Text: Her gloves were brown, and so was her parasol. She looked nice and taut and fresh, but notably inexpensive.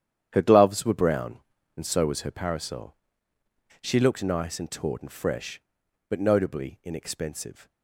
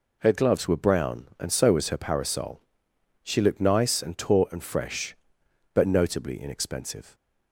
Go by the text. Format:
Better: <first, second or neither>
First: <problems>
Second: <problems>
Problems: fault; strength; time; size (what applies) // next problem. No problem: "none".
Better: second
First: gets quieter; strong; throughout; 12 dB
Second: none